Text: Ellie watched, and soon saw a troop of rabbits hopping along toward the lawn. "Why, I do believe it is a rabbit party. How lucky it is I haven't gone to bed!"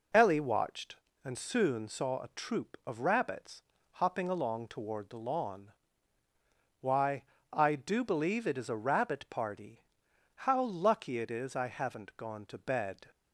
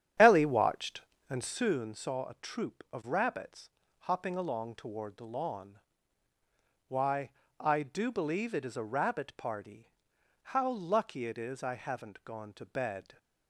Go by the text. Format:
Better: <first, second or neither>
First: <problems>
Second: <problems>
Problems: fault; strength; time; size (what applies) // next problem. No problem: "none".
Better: first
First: pauses between "rabbits" and "hopping"; slight; at 3.6 s; 0.30 s long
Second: starts louder than the rest; strong; until 1.6 s; 9.5 dB // pauses between "rabbits" and "hopping"; slight; at 3.6 s; 0.30 s long